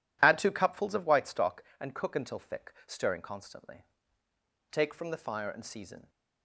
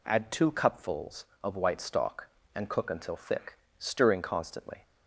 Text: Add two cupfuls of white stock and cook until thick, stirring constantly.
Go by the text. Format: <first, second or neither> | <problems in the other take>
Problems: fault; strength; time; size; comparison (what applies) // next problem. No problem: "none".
second | goes on to say "Take from the fire and season"; from 4.7 s on; 1.3 s long